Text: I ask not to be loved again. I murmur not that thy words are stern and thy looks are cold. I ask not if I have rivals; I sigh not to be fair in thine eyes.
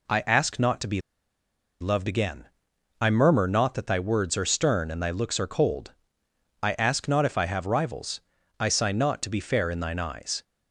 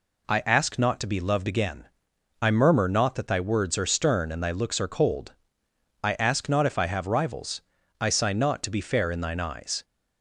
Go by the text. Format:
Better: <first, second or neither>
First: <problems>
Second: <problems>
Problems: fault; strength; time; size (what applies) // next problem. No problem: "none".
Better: second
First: pauses between "be" and "loved"; noticeable; at 1.0 s; 0.79 s long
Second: none